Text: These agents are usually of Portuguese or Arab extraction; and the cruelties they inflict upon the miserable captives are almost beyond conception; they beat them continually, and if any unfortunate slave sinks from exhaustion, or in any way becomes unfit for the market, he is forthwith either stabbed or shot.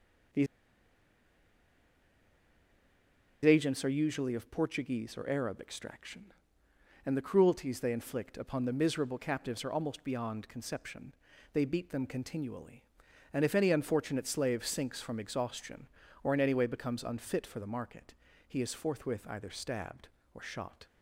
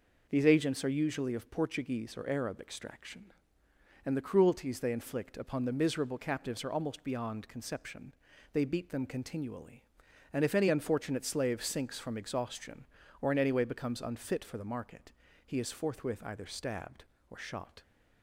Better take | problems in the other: second | pauses between "These" and "agents"; strong; at 0.4 s; 2.9 s long

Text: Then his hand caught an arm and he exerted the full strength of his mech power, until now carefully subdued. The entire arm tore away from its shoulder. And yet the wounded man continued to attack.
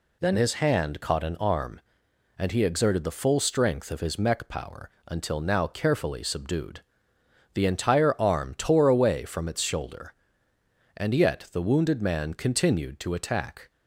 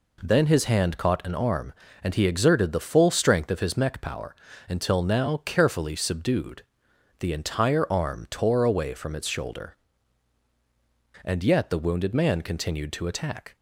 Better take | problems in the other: neither | none

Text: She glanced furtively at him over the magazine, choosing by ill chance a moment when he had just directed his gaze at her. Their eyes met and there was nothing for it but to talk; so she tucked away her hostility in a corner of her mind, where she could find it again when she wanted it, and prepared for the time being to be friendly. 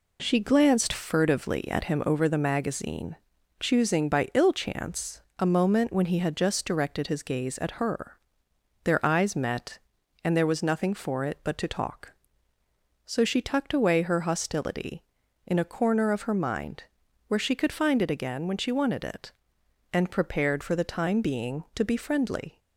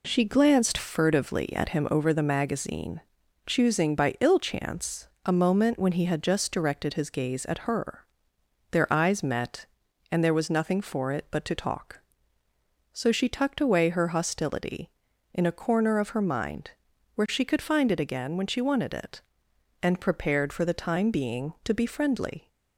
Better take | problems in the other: neither | pauses between "chance" and "a"; slight; the same in both

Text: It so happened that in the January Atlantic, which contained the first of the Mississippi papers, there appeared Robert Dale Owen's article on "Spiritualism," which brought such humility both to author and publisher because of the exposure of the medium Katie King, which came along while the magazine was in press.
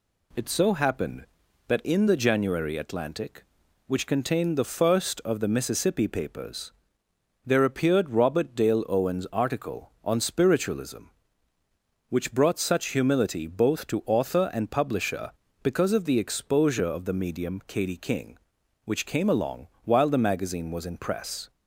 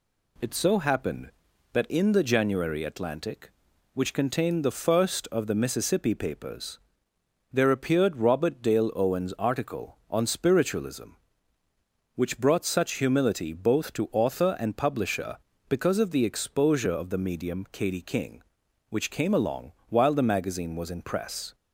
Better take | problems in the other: neither | pauses between "along" and "while"; slight; the same in both

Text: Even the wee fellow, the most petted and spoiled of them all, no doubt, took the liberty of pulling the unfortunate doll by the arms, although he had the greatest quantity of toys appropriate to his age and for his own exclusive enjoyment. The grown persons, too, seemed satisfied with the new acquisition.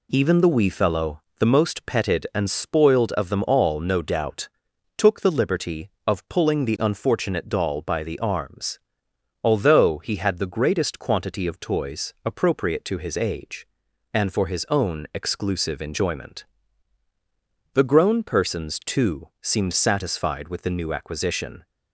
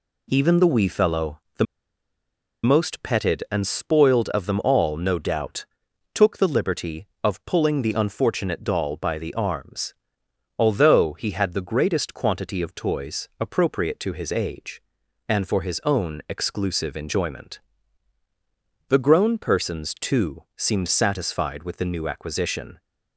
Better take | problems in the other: first | pauses between "the" and "most"; at 1.6 s; 0.98 s long

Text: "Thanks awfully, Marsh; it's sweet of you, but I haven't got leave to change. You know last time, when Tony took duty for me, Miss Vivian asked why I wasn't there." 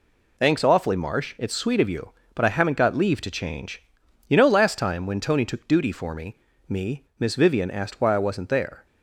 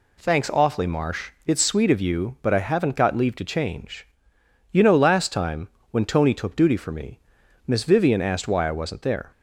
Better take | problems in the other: second | says "me" twice; at 6.6 s

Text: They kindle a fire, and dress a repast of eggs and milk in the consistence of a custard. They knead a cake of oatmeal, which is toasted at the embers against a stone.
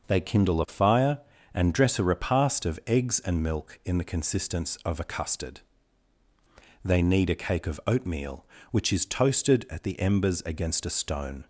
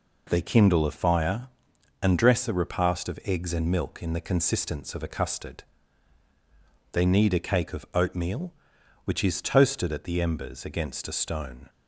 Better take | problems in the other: neither | none

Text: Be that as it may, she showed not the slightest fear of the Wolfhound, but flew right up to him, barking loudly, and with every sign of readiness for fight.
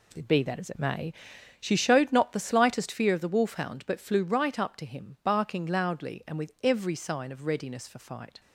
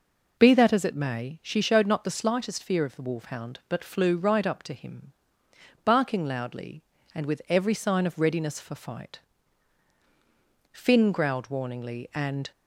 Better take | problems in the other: first | goes on to say "Finn growled warningly and"; strong; from 10.7 s on; 1.7 s long

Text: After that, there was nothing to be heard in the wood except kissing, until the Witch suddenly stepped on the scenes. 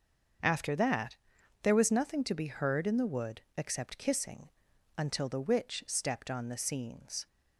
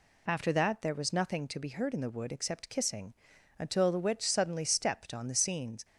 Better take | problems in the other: second | starts louder than the rest; until 1.8 s; 6.5 dB // pauses between "wood" and "except"; slight; at 3.4 s; 0.16 s long // skips "suddenly"; at 5.8 s

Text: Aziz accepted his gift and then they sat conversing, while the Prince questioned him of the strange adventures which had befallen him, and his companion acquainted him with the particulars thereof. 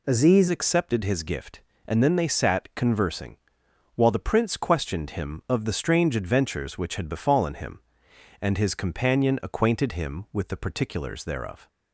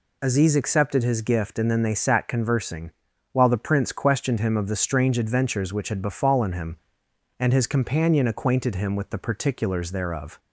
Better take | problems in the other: second | changes voice at "accepted"; from 0.4 s on; 11.2 s long

